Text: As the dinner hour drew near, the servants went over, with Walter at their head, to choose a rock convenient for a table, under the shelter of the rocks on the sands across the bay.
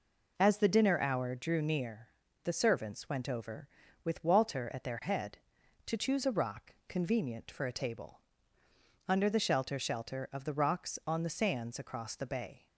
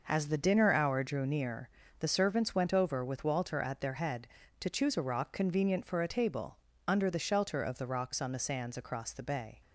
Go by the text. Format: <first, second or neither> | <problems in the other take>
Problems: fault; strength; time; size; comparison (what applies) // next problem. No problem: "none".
second | says "shelter" twice; at 9.7 s